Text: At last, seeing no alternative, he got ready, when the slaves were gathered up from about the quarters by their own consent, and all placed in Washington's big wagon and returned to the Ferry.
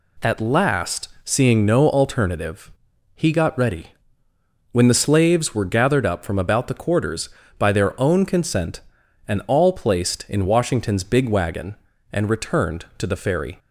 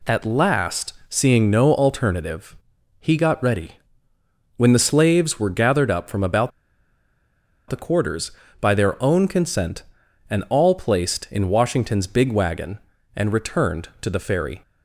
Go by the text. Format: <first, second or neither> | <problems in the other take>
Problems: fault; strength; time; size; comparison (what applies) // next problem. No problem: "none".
first | pauses between "about" and "the"; at 6.5 s; 1.1 s long